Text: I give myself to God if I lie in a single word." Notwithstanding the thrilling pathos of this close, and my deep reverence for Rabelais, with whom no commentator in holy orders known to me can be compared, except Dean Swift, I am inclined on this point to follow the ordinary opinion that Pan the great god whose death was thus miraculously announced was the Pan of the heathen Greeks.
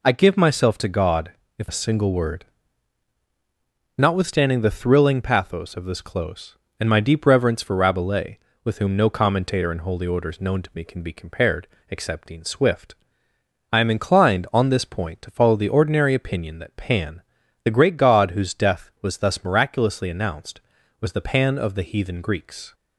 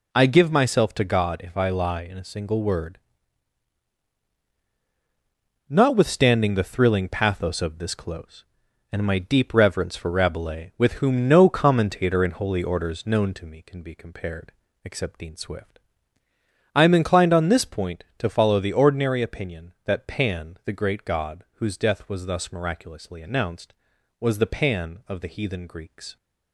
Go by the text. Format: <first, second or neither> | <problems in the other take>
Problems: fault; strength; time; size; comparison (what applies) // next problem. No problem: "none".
second | pauses between "God" and "if"; slight; at 1.3 s; 0.26 s long // skips "I lie in"; at 1.6 s // pauses between "Pan" and "the"; at 17.2 s; 0.42 s long